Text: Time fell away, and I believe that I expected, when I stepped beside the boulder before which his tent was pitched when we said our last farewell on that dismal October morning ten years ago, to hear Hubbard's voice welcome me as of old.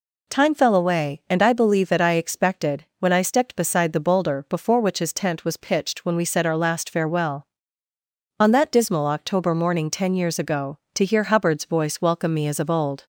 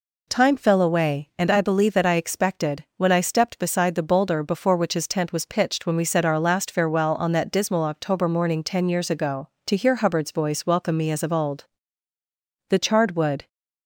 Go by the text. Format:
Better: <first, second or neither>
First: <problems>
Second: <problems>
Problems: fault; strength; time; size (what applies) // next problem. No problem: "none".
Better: first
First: none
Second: goes on to say "The charred wood"; noticeable; from 12.6 s on; 0.80 s long